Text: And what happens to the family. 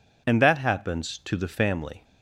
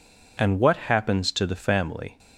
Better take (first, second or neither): second